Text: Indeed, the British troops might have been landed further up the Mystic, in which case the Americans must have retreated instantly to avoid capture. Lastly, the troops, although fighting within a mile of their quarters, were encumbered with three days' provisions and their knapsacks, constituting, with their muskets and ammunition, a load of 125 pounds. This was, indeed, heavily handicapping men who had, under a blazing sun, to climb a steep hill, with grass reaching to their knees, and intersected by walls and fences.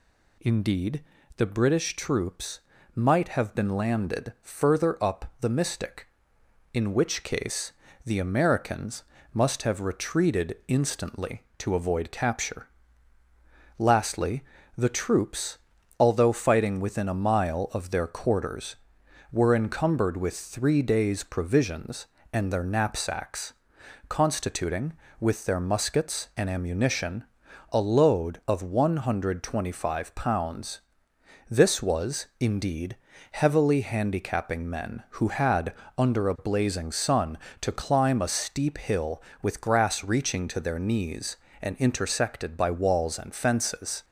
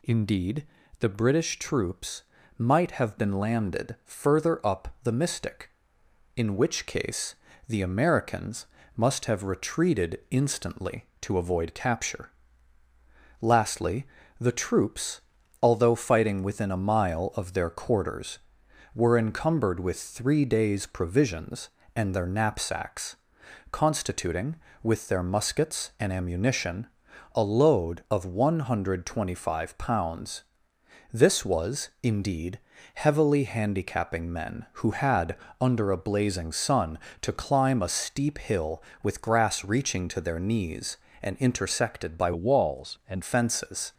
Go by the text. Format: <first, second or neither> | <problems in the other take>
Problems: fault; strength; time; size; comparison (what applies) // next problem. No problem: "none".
first | pauses between "troops" and "might"; slight; at 2.2 s; 0.34 s long; slight in the first // pauses between "case" and "the"; slight; at 7.3 s; 0.32 s long; slight in the first // pauses between "Americans" and "must"; slight; at 8.6 s; 0.30 s long; slight in the first // changes voice from "walls" to "and"; from 42.3 to 43.2 s; 0.9 s long